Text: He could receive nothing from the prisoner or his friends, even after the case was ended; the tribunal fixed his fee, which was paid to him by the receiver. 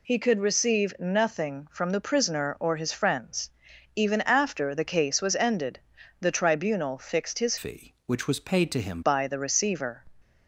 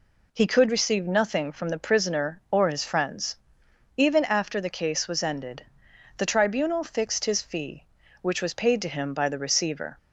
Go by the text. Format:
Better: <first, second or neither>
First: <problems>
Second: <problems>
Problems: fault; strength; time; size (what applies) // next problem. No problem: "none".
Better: second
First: changes voice from "fee" to "him"; from 7.5 to 9.0 s; 1.5 s long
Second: none